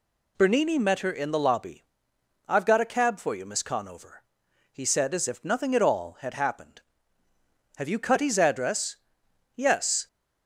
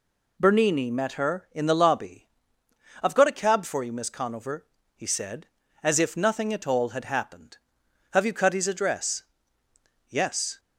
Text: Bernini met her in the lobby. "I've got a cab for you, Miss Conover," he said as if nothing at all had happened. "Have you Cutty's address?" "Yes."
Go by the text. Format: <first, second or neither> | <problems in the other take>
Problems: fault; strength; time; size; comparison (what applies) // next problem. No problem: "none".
neither | none